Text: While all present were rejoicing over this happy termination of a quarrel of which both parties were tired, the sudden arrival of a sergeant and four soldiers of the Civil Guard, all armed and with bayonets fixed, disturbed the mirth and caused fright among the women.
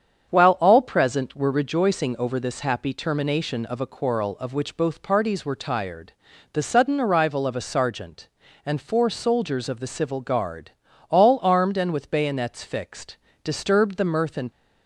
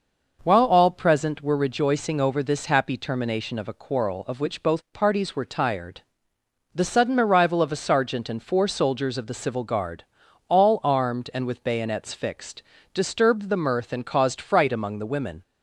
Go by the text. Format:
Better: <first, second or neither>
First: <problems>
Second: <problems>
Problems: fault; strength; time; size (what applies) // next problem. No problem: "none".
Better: second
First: starts louder than the rest; strong; until 1.3 s; 7.5 dB // stops before "caused fright among the women"; at 14.4 s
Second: none